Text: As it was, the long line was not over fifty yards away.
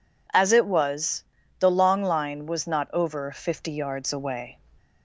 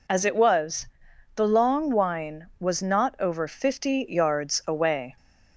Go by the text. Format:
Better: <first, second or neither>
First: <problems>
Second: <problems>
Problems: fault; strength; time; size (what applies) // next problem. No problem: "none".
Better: first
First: none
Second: says "wine" for "line"; at 1.8 s